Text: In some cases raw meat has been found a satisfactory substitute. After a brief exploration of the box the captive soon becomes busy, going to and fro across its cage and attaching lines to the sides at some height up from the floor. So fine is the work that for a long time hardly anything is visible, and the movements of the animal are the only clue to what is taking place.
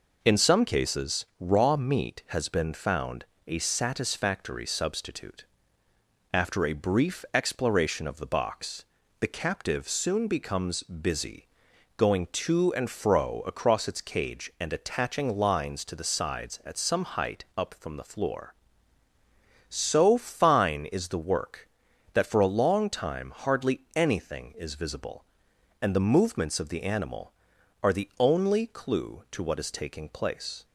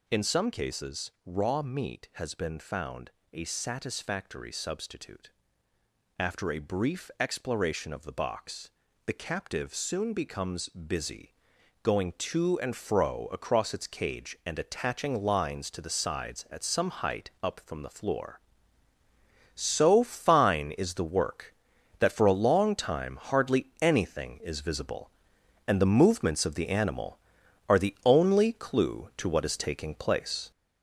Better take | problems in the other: first | gets louder; noticeable; throughout; 6 dB // pauses between "found" and "a"; slight; at 3.1 s; 0.22 s long; slight in the first // pauses between "box" and "the"; slight; at 8.7 s; 0.36 s long; slight in the first

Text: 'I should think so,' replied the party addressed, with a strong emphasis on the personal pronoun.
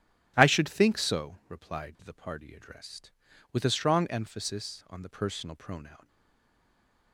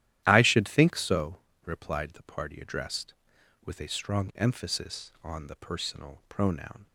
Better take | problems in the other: second | starts louder than the rest; strong; until 1.3 s; 14 dB; strong in the second // stays silent after the last word; from 6.0 s on; 1.1 s long

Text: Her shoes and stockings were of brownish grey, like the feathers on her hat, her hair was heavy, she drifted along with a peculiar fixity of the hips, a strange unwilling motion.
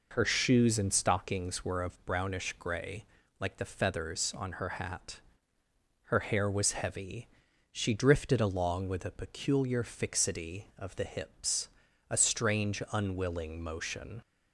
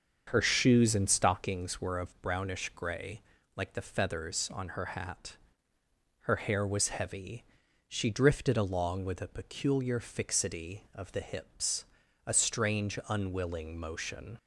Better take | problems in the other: first | starts louder than the rest; until 1.6 s; 7 dB

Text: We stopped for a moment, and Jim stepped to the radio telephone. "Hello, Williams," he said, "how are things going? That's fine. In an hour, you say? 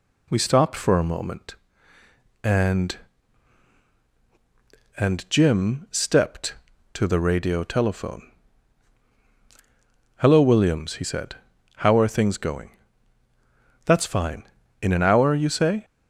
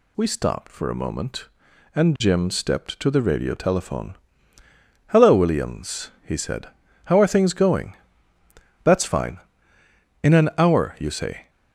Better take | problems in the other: second | says "and" twice; at 4.9 s

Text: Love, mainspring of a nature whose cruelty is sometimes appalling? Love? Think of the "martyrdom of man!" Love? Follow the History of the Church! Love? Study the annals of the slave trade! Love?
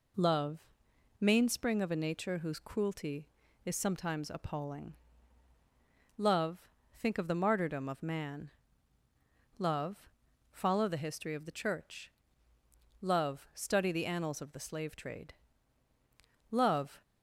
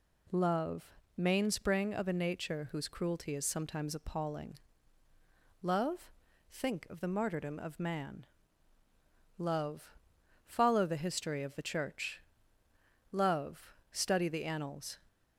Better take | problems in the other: first | stops before "of the slave trade Love"; at 15.0 s

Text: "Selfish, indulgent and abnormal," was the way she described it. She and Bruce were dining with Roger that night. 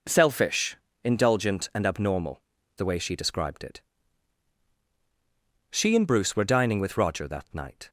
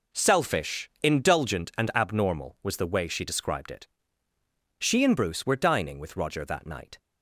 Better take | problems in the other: second | skips "was"; at 2.5 s

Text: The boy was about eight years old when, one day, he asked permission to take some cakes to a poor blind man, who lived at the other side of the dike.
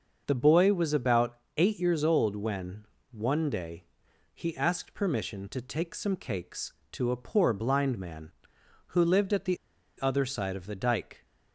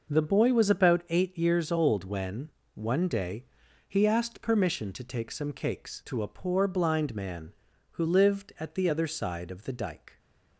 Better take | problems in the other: second | starts louder than the rest; noticeable; until 1.2 s; 6 dB // pauses between "about" and "eight"; slight; at 1.3 s; 0.20 s long // pauses between "the" and "other"; at 9.5 s; 0.44 s long

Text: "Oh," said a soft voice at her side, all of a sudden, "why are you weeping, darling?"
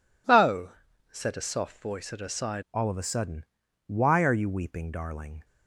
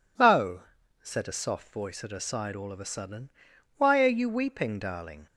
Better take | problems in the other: second | changes voice at "all"; from 2.7 s on; 2.7 s long

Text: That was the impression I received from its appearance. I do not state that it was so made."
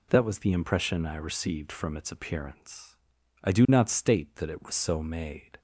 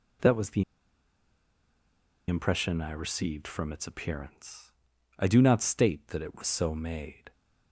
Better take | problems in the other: first | pauses between "the" and "impression"; strong; at 0.6 s; 1.6 s long

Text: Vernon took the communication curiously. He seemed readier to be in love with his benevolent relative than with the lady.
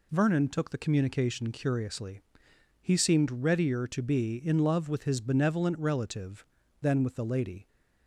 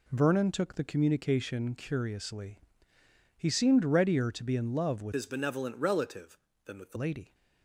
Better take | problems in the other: first | changes voice from "his" to "the"; from 5.1 to 6.9 s; 1.8 s long

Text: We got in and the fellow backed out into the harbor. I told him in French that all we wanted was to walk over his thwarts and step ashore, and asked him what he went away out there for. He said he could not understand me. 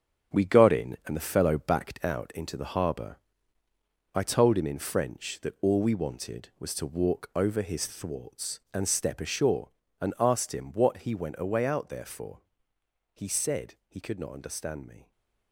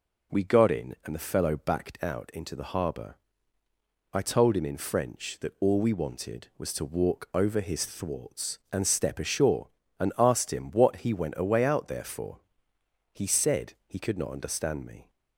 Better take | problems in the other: second | gets quieter; strong; throughout; 8.5 dB

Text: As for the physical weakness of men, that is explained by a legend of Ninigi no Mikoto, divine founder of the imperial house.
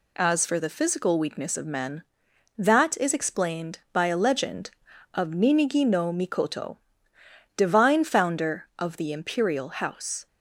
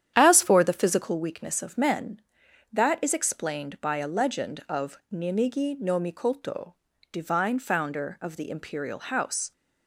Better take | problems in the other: first | starts louder than the rest; strong; until 1.2 s; 9.5 dB

